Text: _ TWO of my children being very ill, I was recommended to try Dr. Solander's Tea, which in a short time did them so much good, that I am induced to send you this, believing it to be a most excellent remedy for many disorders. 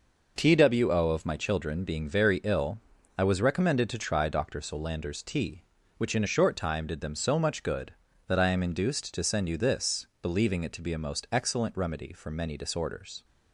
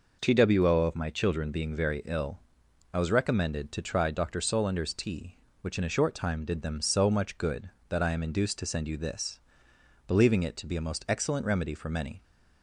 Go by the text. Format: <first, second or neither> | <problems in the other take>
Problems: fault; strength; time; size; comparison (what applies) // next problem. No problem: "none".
first | stops before "disorders"; at 12.2 s